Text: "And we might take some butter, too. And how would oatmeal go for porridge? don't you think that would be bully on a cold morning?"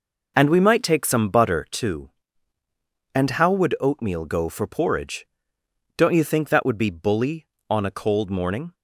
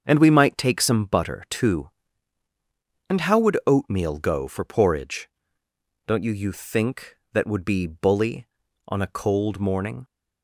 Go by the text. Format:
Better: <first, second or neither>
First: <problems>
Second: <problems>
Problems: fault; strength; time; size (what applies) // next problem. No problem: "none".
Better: first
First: none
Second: starts louder than the rest; until 1.0 s; 7 dB // says "you" twice; at 6.3 s